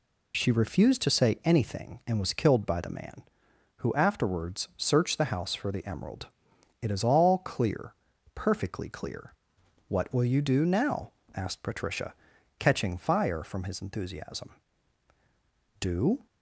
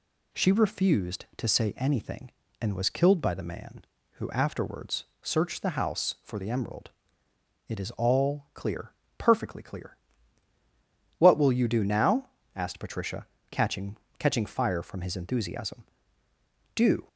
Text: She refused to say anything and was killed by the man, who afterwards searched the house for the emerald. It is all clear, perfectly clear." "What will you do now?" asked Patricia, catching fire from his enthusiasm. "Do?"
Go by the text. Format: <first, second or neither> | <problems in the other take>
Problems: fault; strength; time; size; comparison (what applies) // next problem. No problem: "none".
first | pauses between "afterwards" and "searched"; slight; at 5.0 s; 0.16 s long // says "catching" twice; at 14.1 s